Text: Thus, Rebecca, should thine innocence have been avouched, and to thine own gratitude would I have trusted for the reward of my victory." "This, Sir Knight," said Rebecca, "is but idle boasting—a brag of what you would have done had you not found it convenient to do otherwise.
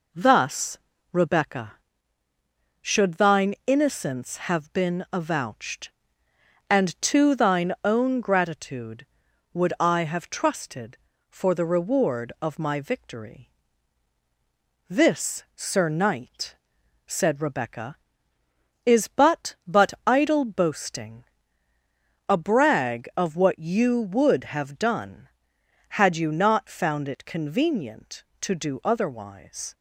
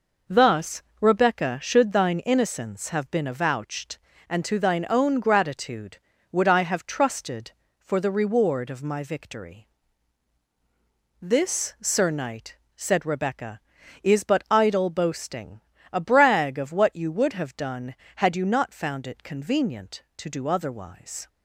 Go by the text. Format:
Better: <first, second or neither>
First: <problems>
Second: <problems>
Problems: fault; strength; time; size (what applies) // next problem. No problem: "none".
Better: second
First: says "but" twice; at 19.6 s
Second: none